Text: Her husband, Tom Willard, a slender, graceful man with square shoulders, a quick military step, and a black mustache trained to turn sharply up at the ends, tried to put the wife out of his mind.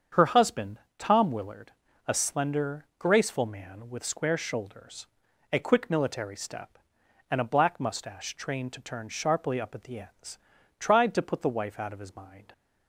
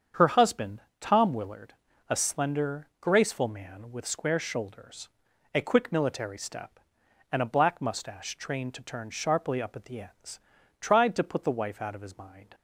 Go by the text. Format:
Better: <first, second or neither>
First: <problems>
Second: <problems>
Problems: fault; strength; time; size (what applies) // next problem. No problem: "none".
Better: neither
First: starts louder than the rest; strong; until 1.3 s; 7.5 dB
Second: starts louder than the rest; strong; until 1.3 s; 7.5 dB